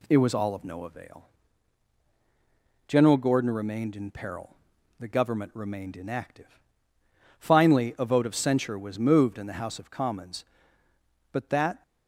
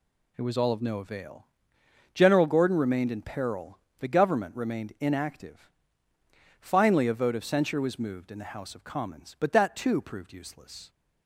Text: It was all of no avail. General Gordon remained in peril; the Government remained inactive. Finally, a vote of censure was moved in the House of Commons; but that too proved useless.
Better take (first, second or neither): second